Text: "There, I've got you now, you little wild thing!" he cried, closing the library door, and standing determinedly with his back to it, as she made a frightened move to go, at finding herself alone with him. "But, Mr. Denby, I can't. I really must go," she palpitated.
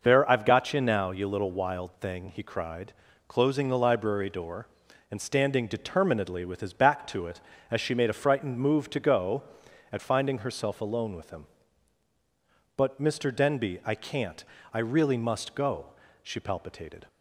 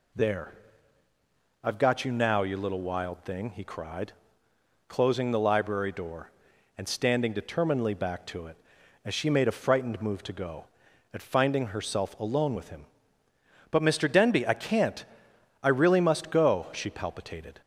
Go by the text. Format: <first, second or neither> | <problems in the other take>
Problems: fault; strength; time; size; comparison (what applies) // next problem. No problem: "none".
first | skips "with his"; at 7.9 s